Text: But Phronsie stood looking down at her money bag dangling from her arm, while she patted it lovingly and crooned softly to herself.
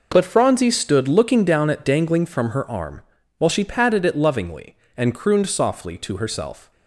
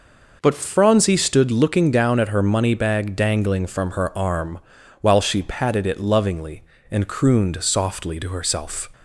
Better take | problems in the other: second | skips "her money bag"; at 1.8 s

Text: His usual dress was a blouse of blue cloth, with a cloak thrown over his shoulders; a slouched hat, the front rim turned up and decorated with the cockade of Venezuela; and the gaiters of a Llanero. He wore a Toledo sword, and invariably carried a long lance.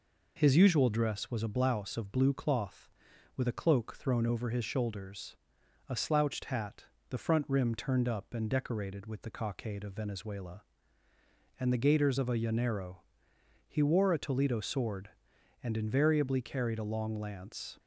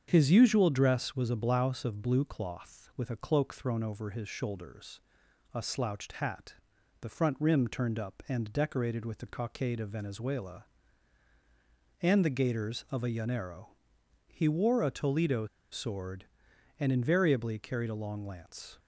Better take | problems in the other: first | starts louder than the rest; strong; until 1.0 s; 7.5 dB // pauses between "Toledo" and "sword"; slight; at 15.4 s; 0.26 s long

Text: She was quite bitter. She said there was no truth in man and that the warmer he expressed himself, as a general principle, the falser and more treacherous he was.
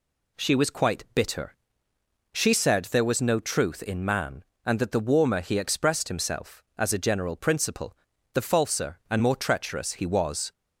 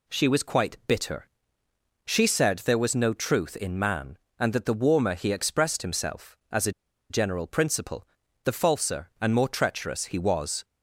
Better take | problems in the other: first | pauses between "a" and "general"; at 6.7 s; 0.38 s long

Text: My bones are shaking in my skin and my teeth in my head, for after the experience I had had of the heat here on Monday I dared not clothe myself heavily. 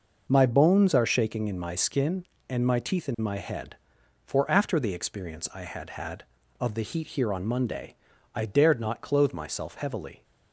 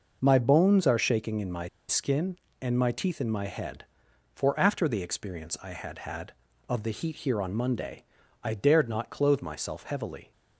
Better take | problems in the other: first | pauses between "my" and "skin"; slight; at 1.6 s; 0.20 s long // pauses between "Monday" and "I"; at 8.0 s; 0.38 s long; also in the first

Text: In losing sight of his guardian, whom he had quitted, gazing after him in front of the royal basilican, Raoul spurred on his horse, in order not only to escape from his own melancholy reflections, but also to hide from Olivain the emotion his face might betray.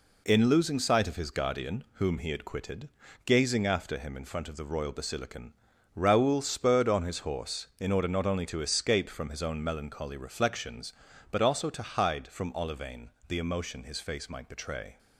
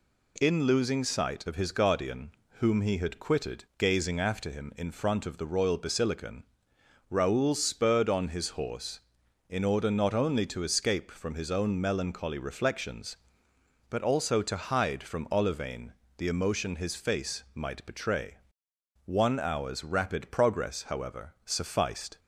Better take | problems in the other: first | pauses between "Olivain" and "the"; slight; at 15.9 s; 0.26 s long; slight in the first // goes on to say "One hour's rapid progress however sufficed"; strong; from 19.0 s on; 3.1 s long

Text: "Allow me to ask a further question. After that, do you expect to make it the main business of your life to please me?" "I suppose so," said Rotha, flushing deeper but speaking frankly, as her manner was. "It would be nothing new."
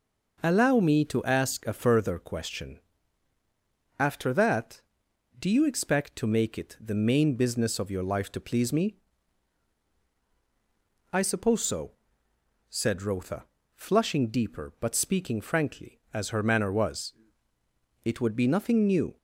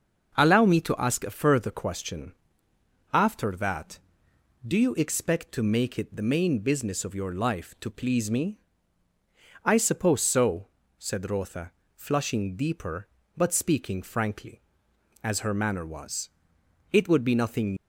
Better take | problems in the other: first | starts louder than the rest; until 1.4 s; 6.5 dB // stops before "new"; at 17.7 s

